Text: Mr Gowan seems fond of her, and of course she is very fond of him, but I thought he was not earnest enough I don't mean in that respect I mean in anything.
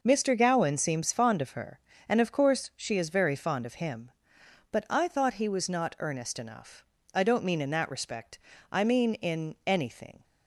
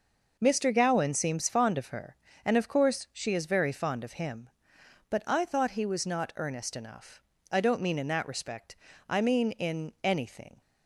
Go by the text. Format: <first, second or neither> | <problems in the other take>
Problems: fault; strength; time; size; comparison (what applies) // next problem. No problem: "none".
neither | pauses between "enough" and "I"; slight; the same in both // pauses between "respect" and "I"; slight; the same in both